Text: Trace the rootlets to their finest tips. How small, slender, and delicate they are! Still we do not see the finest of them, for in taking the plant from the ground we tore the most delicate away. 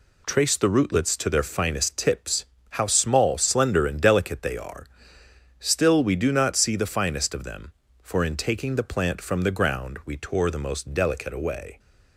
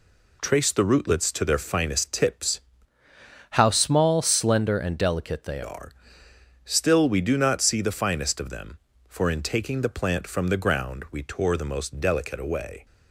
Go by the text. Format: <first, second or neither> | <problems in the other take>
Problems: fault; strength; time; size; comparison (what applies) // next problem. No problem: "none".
first | changes voice from "How" to "they"; from 3.5 to 5.6 s; 2.1 s long